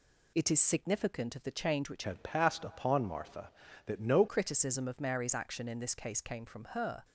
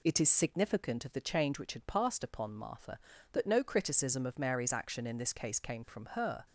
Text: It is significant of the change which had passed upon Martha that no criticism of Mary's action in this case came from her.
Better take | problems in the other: second | changes voice from "had" to "no"; from 2.0 to 4.2 s; 2.2 s long

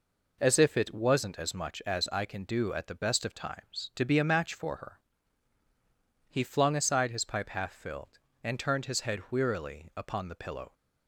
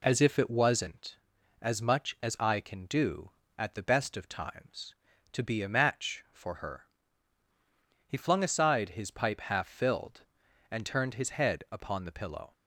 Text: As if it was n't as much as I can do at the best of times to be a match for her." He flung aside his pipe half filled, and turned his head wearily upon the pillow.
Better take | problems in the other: first | skips "wearily"; at 11.6 s

